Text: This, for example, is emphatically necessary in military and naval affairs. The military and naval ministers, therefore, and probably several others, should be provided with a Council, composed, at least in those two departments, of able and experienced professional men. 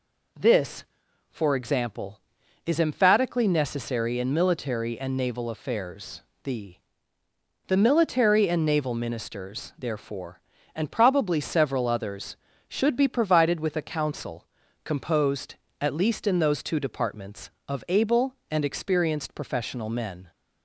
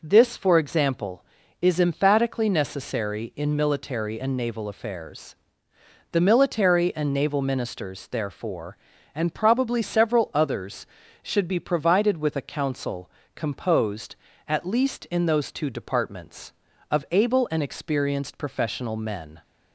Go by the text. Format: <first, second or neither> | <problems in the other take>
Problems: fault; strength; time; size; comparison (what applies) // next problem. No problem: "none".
second | says "The" twice; at 7.6 s